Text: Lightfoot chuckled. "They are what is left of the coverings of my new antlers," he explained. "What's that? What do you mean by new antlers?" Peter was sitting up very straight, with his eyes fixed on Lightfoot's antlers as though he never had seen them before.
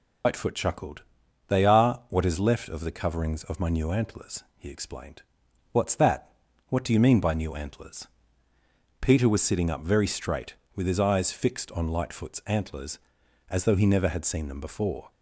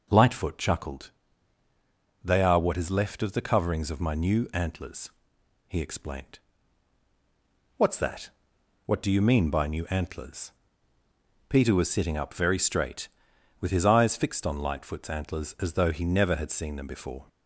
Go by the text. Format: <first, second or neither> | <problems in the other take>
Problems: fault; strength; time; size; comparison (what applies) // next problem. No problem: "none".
second | loses the start of "Lightfoot"; at 0.2 s; 115 ms